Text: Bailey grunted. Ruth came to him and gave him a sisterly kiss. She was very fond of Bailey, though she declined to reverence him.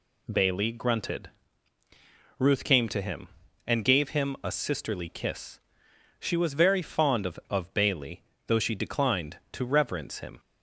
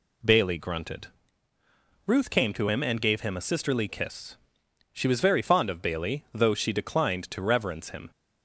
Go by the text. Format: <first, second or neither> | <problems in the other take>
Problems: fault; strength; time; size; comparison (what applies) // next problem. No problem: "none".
second | says "of" twice; at 7.5 s